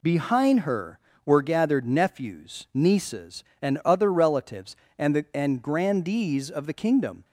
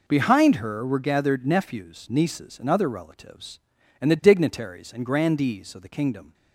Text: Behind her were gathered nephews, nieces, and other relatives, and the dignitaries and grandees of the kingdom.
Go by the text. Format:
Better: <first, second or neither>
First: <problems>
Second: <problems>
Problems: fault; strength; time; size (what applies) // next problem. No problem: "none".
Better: second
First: skips "dignitaries"; at 5.2 s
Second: none